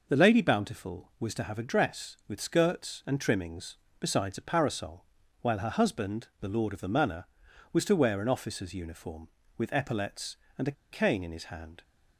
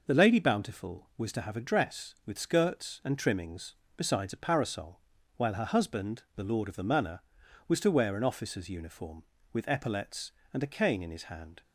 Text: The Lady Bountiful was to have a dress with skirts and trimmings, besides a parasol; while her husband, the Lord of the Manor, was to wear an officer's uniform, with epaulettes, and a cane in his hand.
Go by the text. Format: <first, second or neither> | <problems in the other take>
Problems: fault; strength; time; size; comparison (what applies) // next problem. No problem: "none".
second | pauses between "a" and "cane"; slight; at 10.7 s; 0.19 s long